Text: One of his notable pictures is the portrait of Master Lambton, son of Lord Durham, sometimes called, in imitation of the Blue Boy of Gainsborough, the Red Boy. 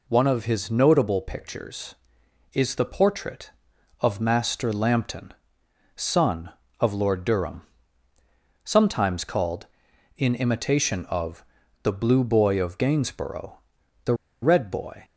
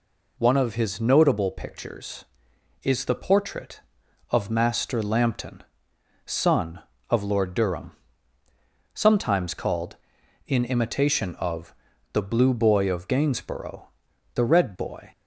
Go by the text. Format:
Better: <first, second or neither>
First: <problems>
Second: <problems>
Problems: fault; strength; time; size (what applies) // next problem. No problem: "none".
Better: second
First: pauses between "of" and "the"; at 11.4 s; 0.38 s long // pauses between "the" and "Red"; slight; at 14.1 s; 0.28 s long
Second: pauses between "of" and "the"; at 11.7 s; 0.38 s long